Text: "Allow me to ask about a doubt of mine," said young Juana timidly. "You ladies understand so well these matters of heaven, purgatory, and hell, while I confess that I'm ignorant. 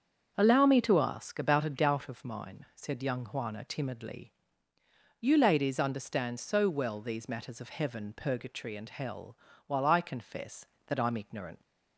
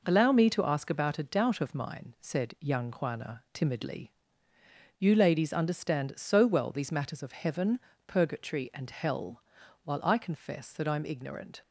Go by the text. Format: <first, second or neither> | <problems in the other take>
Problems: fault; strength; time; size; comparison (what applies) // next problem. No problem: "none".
second | starts louder than the rest; until 1.3 s; 7 dB // leaves "ignorant" unfinished; at 11.6 s; 70 ms